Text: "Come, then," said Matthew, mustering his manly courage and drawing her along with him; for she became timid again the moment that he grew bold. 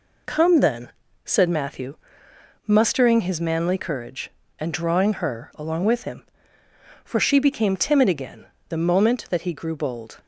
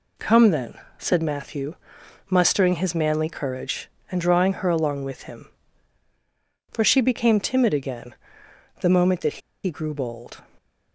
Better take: first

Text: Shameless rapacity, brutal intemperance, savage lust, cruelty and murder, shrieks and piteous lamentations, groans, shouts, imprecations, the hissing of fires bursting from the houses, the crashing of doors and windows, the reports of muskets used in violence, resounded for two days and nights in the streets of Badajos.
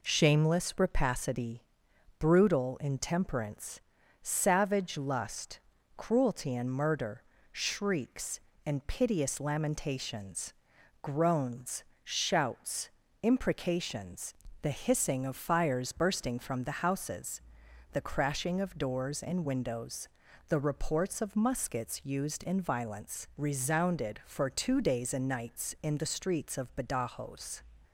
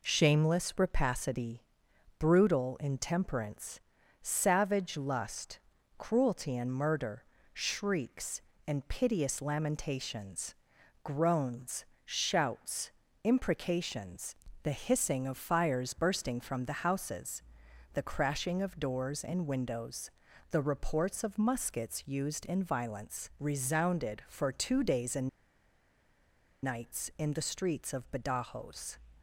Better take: first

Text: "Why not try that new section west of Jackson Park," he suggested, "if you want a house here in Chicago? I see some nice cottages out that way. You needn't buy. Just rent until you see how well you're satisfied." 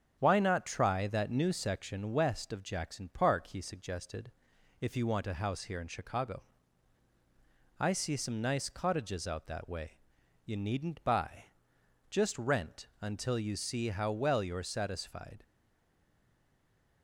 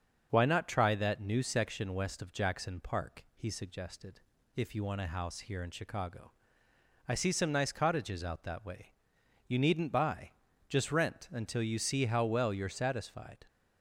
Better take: second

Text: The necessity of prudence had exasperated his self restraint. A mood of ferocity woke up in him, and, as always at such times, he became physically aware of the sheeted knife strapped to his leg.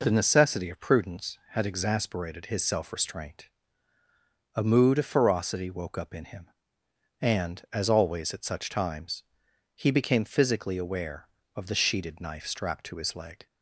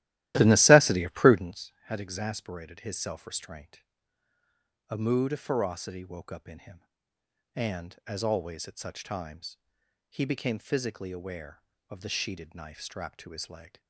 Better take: first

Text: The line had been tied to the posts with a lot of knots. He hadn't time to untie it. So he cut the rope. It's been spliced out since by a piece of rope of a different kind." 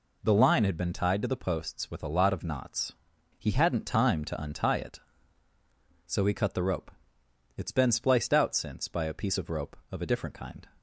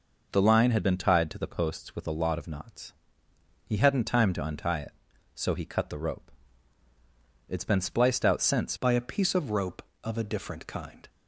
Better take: first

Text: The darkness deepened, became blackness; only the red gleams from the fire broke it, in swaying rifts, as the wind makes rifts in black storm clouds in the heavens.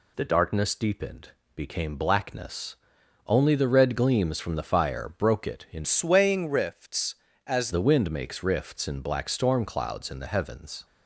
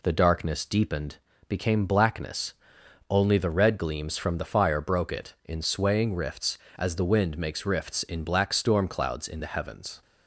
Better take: second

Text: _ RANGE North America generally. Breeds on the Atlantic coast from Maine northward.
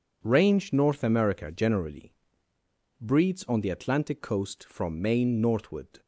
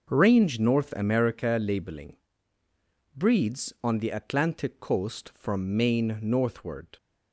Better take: first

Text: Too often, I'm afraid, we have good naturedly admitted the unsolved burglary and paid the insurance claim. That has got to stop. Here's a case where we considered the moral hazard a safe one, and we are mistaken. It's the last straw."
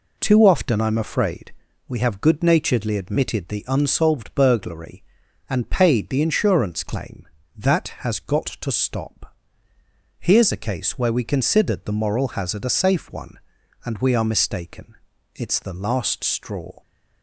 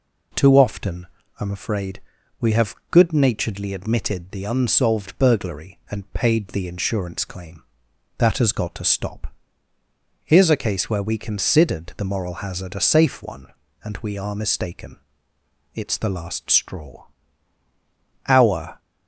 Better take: first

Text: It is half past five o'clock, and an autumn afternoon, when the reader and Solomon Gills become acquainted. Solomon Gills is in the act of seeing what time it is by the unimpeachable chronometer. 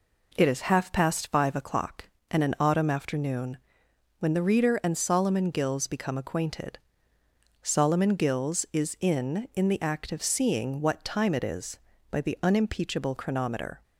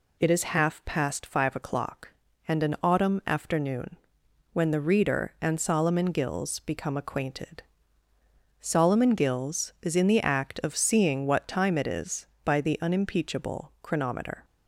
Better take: second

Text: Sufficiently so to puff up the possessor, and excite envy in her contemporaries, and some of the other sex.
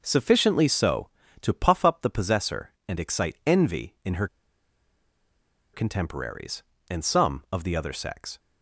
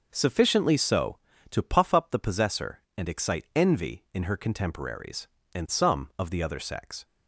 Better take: second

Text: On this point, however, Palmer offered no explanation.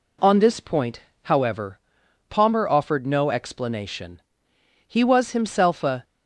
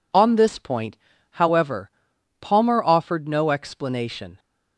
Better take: second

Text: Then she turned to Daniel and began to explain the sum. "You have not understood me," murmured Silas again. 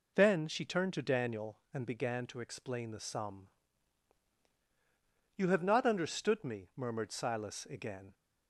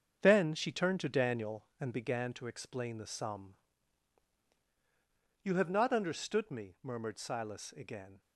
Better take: first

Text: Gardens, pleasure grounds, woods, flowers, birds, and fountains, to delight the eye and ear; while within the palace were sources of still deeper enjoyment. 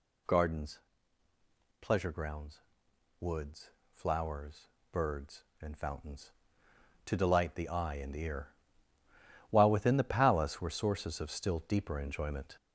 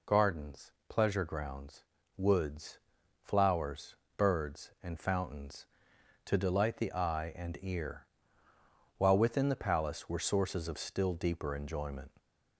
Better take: second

